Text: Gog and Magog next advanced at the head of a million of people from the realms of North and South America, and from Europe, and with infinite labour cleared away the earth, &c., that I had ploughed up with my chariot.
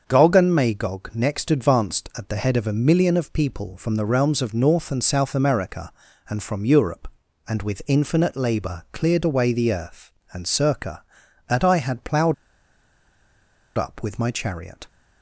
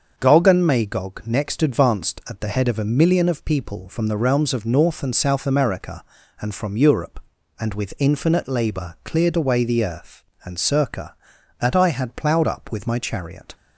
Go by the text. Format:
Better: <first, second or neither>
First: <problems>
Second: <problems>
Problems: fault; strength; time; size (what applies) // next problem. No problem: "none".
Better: second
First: starts louder than the rest; until 1.0 s; 6.5 dB // pauses between "ploughed" and "up"; strong; at 12.3 s; 1.4 s long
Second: starts louder than the rest; until 1.1 s; 6.5 dB